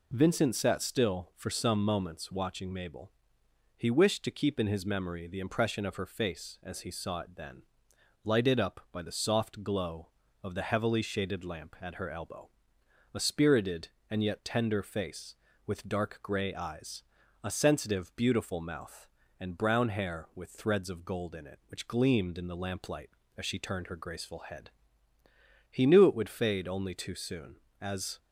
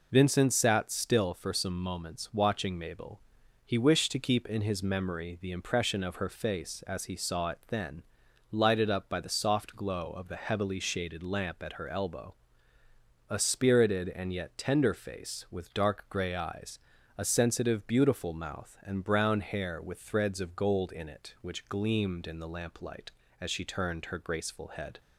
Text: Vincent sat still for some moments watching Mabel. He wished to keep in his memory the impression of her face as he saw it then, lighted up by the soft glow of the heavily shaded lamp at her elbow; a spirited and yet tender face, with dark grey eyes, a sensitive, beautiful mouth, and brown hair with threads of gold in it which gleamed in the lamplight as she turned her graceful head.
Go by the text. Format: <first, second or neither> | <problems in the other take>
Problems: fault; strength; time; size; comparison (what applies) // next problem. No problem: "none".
second | goes on to say "He knew it would fade only too soon as"; strong; from 25.7 s on; 2.4 s long